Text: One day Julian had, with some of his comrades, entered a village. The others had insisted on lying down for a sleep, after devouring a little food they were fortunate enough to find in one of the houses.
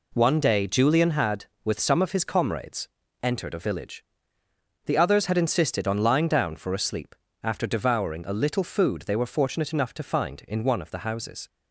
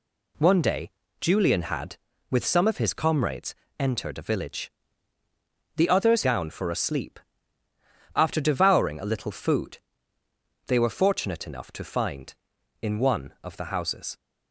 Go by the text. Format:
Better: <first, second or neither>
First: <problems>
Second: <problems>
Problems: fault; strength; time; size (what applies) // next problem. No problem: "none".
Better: first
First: none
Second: pauses between "day" and "Julian"; slight; at 0.8 s; 0.32 s long // skips "had insisted on lying"; at 6.2 s // pauses between "food" and "they"; noticeable; at 9.7 s; 0.90 s long